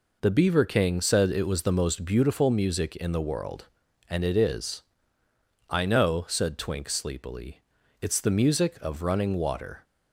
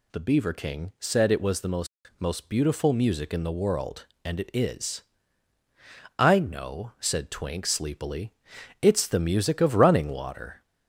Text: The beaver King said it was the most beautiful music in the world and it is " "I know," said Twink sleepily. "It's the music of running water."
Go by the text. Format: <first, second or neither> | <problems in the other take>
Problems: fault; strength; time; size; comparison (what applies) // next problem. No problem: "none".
first | says "most" twice; at 2.1 s